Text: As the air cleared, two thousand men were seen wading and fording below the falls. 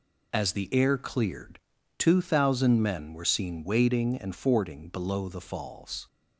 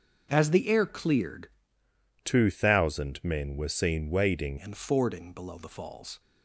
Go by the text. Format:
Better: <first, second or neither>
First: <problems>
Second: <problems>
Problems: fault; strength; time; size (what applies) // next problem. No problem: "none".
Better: first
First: none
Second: starts louder than the rest; noticeable; until 1.3 s; 6 dB // changes voice from "two" to "wading"; from 2.2 to 4.5 s; 2.3 s long